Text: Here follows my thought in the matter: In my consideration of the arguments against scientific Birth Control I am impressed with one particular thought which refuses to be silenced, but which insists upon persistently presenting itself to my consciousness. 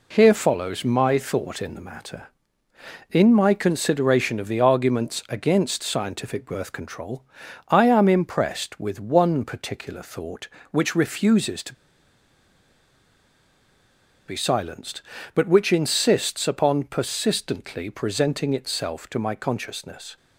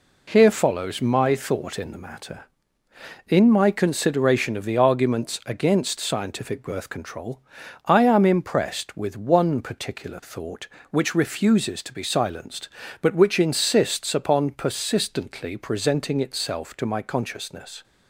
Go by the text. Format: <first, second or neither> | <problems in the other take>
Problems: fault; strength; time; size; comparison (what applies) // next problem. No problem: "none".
second | pauses between "Control" and "I"; noticeable; at 7.2 s; 0.46 s long; noticeable in the second // pauses between "to" and "be"; strong; at 11.7 s; 2.5 s long